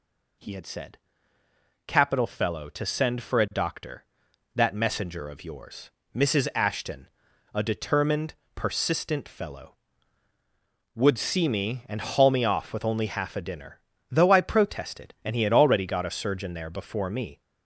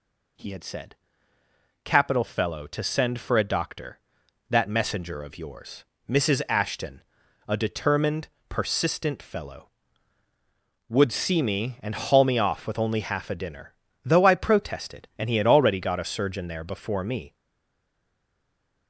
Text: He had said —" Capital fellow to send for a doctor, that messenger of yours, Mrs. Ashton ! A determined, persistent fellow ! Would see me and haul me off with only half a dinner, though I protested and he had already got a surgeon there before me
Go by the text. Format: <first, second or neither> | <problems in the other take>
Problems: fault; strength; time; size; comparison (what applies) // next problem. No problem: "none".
first | stays silent after the last word; noticeable; from 17.3 s on; 1.5 s long